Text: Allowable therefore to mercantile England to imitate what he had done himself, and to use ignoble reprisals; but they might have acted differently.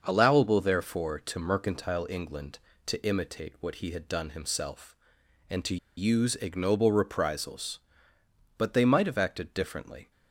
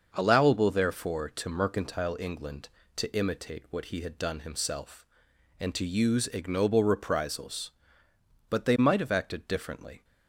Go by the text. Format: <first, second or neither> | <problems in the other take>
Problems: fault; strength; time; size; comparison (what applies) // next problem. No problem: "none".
second | starts louder than the rest; noticeable; until 1.0 s; 6 dB; also in the second // pauses between "to" and "use"; slight; at 5.7 s; 0.21 s long